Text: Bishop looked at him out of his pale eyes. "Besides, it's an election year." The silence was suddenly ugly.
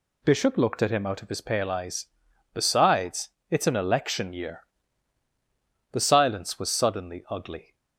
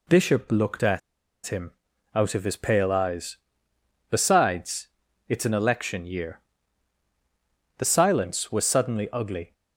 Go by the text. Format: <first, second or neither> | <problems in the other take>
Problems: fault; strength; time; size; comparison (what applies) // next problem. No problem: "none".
first | pauses between "at" and "him"; noticeable; at 0.9 s; 0.46 s long // pauses between "him" and "out"; at 1.7 s; 0.42 s long